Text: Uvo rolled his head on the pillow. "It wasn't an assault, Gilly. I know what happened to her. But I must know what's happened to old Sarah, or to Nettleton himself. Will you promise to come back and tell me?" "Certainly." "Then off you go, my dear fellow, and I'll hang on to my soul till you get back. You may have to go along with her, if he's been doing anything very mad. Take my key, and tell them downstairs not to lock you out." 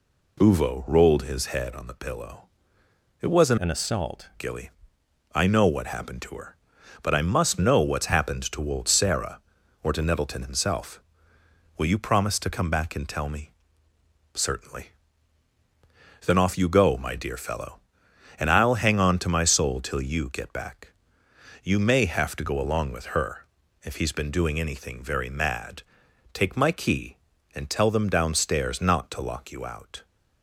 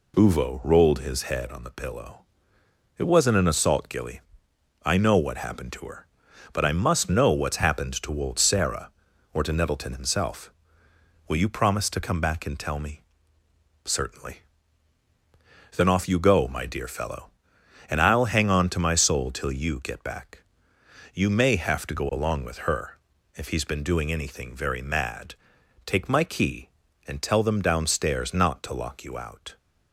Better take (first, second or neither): second